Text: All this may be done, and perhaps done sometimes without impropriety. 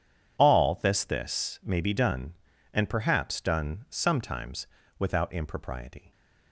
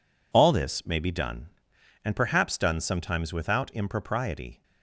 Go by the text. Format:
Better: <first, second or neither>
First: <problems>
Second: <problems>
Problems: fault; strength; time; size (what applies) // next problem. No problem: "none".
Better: second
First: says "this" twice; at 1.0 s // pauses between "sometimes" and "without"; slight; at 4.6 s; 0.32 s long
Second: none